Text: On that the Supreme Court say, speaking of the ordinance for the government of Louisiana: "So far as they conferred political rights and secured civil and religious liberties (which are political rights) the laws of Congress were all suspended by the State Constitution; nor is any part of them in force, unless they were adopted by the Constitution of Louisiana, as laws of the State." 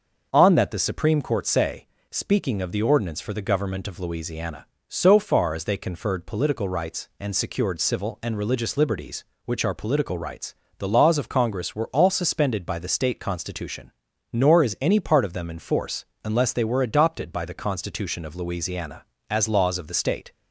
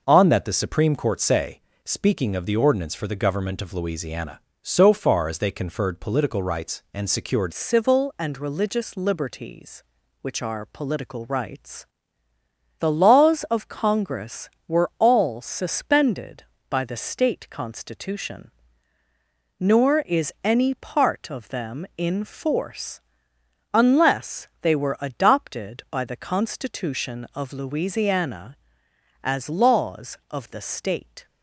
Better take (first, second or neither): first